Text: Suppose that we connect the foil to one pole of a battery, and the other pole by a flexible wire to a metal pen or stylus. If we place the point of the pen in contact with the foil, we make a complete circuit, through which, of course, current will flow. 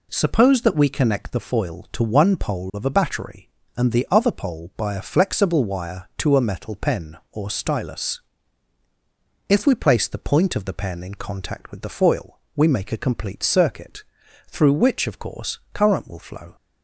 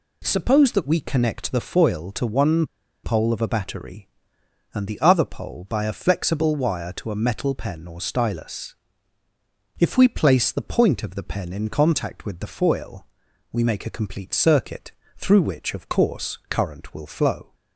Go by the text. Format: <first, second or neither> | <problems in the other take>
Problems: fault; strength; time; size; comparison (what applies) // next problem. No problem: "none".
first | pauses between "one" and "pole"; at 2.6 s; 0.38 s long